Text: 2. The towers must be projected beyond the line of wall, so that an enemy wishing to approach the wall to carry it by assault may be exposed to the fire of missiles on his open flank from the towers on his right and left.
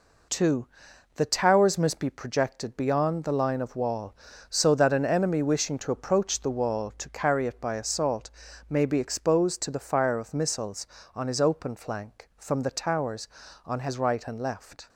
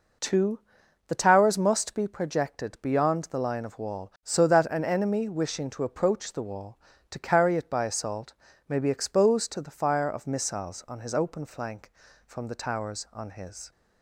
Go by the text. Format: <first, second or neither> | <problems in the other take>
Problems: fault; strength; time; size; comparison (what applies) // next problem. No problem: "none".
first | pauses between "assault" and "may"; slight; at 8.3 s; 0.34 s long; also in the first // stops before "right and left"; at 13.7 s